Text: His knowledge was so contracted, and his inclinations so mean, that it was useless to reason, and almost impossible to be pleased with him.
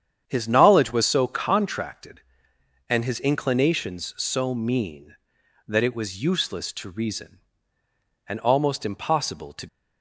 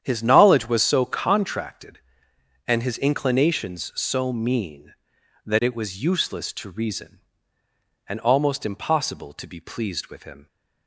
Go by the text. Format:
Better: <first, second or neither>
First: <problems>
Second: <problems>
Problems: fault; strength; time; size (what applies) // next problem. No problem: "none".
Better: second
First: starts louder than the rest; strong; until 1.3 s; 8.5 dB // stops before "be pleased with him"; at 9.6 s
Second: starts louder than the rest; strong; until 1.0 s; 9 dB